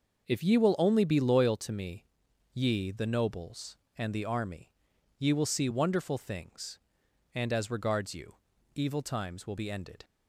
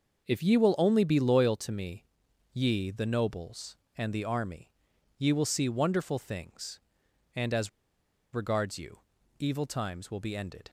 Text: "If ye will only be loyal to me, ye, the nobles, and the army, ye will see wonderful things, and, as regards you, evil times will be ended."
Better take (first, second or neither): first